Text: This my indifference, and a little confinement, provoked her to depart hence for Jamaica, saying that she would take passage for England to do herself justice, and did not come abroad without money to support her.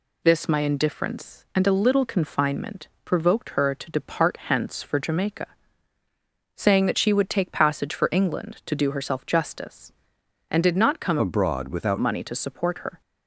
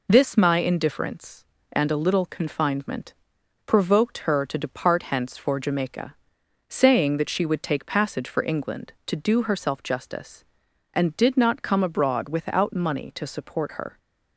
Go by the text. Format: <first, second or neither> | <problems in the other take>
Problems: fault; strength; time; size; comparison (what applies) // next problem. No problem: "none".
second | changes voice from "abroad" to "without"; from 11.1 to 11.9 s; 0.8 s long